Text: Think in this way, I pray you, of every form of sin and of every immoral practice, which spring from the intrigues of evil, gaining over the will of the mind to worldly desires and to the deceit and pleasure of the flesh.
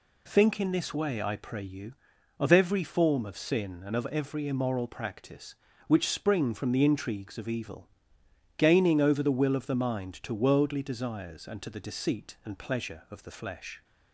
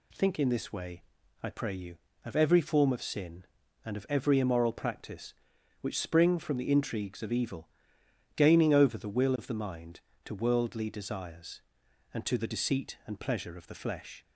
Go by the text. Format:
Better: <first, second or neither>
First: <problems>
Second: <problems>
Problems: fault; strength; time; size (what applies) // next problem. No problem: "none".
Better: neither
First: none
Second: none